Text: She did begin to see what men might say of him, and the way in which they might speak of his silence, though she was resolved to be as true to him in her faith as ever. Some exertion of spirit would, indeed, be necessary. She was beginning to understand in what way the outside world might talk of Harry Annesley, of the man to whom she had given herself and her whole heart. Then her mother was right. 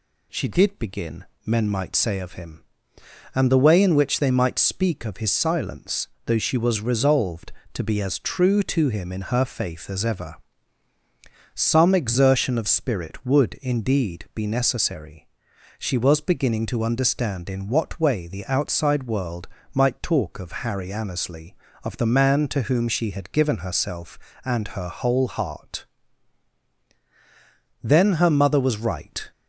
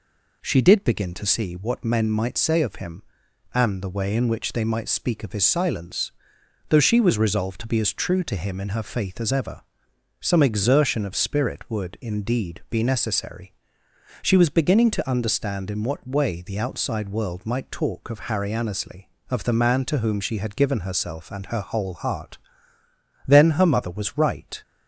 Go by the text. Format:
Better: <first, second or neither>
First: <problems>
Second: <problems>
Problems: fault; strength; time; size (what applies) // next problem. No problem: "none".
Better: second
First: skips "to see what"; at 1.3 s // pauses between "world" and "might"; slight; at 19.4 s; 0.26 s long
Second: none